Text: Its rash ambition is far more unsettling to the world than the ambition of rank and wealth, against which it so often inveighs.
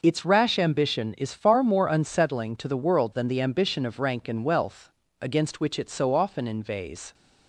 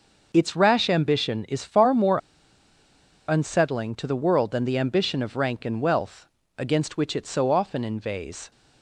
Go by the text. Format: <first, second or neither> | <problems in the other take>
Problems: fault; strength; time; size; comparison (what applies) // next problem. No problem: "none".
first | pauses between "more" and "unsettling"; at 2.1 s; 1.1 s long